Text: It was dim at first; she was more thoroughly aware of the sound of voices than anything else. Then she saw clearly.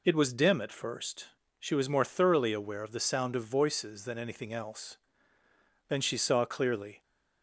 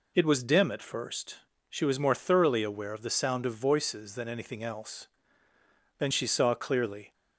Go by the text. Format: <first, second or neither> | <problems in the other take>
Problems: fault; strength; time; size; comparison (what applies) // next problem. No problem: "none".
neither | none